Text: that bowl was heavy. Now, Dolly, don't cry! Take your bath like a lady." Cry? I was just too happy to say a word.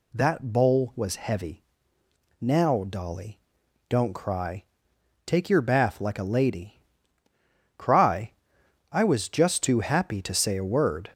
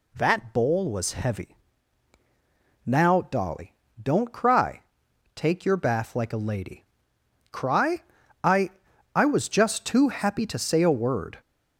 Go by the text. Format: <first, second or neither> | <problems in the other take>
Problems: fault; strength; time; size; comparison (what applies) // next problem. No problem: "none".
first | says "I" twice; at 9.1 s